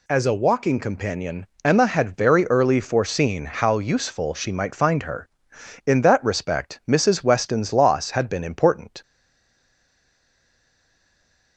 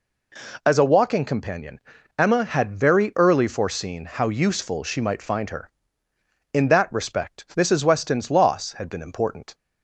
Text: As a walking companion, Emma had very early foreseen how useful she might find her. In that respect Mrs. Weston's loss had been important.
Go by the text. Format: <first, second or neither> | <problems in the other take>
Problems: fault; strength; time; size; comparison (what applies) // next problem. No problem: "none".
second | stays silent after the last word; strong; from 9.0 s on; 2.5 s long